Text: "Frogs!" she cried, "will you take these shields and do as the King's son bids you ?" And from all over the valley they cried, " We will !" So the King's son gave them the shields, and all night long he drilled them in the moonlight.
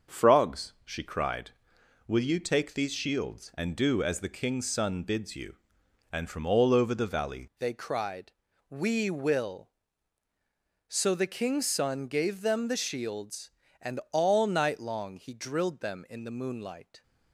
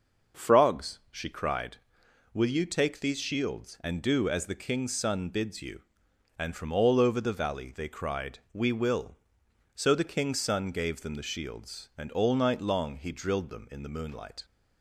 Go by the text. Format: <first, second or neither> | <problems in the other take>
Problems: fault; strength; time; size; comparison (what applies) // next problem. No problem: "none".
second | starts louder than the rest; until 1.2 s; 6.5 dB; also in the second // changes voice at "they"; from 7.5 s on; 9.5 s long